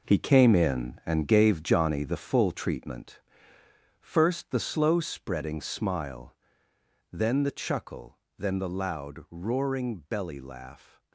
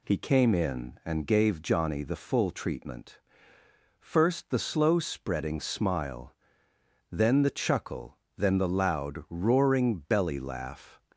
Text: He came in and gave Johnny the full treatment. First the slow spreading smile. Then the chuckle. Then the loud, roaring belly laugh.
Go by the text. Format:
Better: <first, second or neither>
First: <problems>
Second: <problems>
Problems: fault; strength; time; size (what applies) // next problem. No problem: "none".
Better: second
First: gets quieter; strong; throughout; 9.5 dB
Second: none